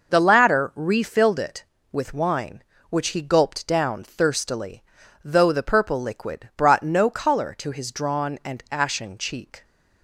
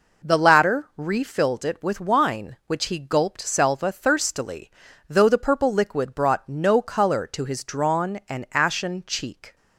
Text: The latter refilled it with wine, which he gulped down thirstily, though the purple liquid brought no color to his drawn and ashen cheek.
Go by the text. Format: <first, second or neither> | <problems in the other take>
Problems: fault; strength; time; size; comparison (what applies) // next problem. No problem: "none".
first | says "selva" for "down"; at 3.4 s